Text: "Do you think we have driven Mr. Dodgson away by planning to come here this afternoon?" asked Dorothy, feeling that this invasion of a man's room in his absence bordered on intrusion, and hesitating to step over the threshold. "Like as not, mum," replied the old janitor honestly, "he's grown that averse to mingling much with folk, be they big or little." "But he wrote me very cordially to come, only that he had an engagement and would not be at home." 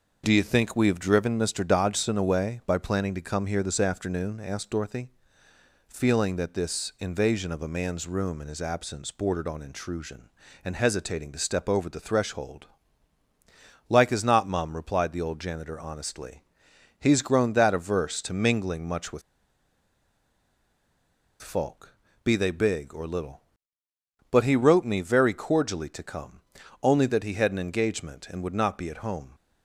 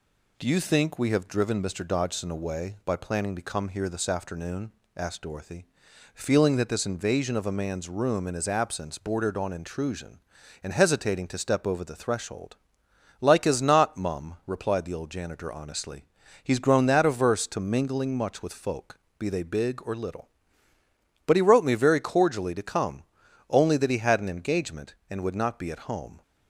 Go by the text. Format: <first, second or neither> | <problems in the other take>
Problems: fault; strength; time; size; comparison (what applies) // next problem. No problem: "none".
second | pauses between "with" and "folk"; strong; at 19.2 s; 2.2 s long